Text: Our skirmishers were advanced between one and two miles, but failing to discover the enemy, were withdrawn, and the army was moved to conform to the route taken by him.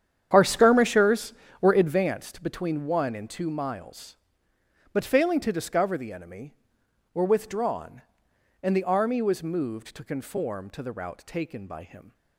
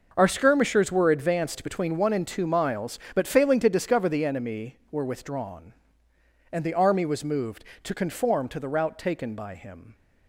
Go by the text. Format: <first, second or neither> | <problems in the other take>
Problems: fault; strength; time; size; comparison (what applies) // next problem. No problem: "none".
second | starts louder than the rest; strong; until 2.1 s; 9 dB